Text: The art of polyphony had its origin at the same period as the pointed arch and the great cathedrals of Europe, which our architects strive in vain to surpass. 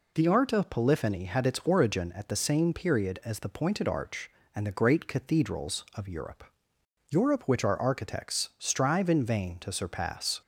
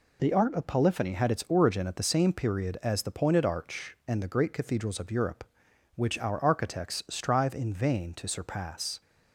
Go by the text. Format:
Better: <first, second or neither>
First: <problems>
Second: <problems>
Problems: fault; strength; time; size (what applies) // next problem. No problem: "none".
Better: second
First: says "Europe" twice; at 7.0 s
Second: none